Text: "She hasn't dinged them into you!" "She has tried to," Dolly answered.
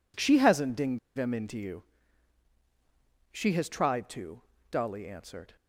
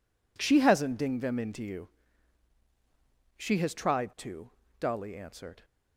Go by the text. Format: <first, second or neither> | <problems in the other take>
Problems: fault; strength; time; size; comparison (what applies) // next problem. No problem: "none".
second | pauses between "dinged" and "them"; slight; at 0.9 s; 0.18 s long